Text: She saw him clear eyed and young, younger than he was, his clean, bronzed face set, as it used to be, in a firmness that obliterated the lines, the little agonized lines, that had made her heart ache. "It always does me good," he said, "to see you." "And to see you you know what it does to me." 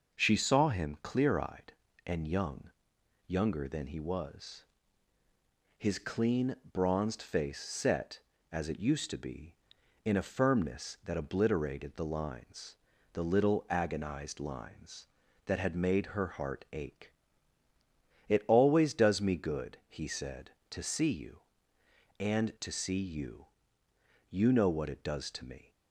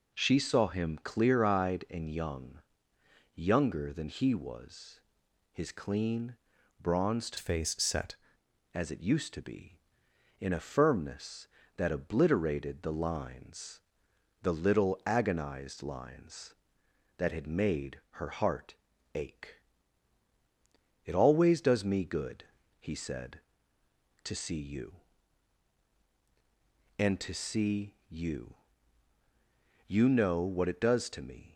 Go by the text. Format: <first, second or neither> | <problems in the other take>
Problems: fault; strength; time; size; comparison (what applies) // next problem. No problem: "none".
first | changes voice from "face" to "set"; from 7.3 to 8.1 s; 0.8 s long // pauses between "heart" and "ache"; at 18.7 s; 0.38 s long // pauses between "you" and "you"; strong; at 28.5 s; 1.3 s long; noticeable in the first